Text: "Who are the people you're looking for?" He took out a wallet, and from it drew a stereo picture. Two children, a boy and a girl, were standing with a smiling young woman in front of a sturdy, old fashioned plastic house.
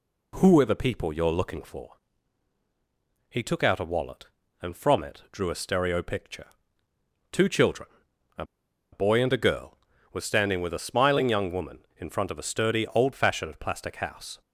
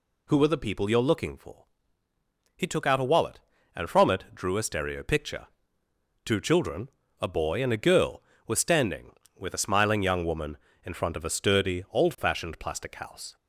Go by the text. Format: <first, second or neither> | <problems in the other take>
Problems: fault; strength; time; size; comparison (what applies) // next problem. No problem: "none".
second | pauses between "a" and "boy"; noticeable; at 8.4 s; 0.48 s long